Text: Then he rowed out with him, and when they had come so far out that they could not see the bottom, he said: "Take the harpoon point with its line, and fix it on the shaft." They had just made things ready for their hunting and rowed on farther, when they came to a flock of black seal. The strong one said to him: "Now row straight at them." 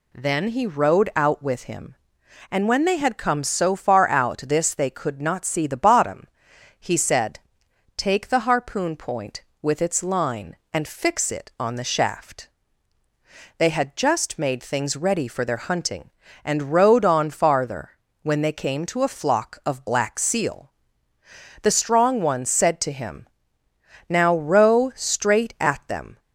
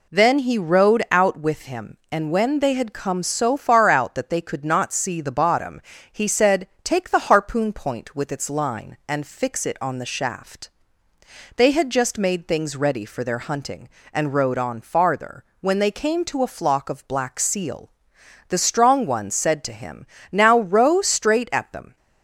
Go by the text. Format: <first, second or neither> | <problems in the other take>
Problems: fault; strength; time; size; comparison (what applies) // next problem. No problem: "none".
second | says "this" for "that"; at 4.4 s